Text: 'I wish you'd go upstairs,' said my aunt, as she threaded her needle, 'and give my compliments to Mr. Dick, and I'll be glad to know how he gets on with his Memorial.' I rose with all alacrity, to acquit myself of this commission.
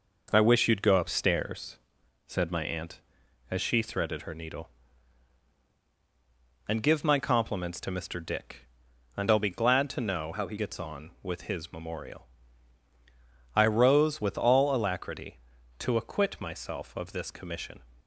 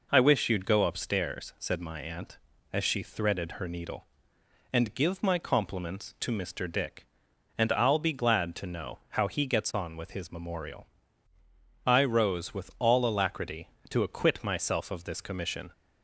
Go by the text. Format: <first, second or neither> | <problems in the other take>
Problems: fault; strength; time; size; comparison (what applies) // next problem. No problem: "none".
second | changes voice from "how" to "he"; from 10.3 to 10.5 s; 0.2 s long